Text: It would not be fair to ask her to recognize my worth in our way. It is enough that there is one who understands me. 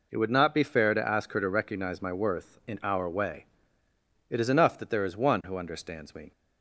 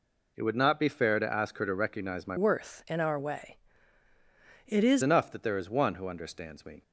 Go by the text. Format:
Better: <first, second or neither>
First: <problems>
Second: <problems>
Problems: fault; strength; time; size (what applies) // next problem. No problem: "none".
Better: first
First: none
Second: changes voice from "worth" to "is"; from 2.3 to 5.0 s; 2.7 s long